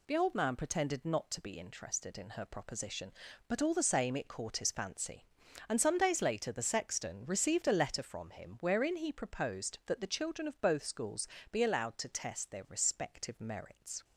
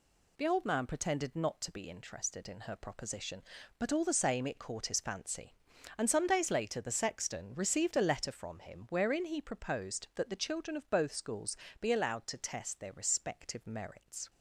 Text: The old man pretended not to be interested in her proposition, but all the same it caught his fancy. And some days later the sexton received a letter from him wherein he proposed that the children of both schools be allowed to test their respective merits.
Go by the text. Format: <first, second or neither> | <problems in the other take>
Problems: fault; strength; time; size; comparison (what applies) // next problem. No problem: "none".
neither | pauses between "schools" and "be"; slight; the same in both